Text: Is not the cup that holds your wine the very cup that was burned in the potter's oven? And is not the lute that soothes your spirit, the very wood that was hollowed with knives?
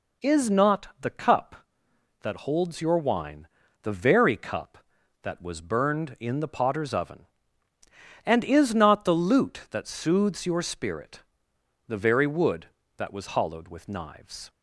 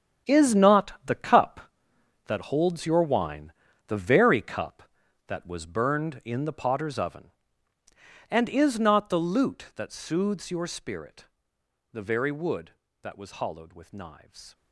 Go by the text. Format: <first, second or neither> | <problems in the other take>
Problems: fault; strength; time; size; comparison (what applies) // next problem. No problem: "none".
first | gets quieter; strong; throughout; 12 dB // pauses between "wine" and "the"; slight; at 3.5 s; 0.36 s long; slight in the first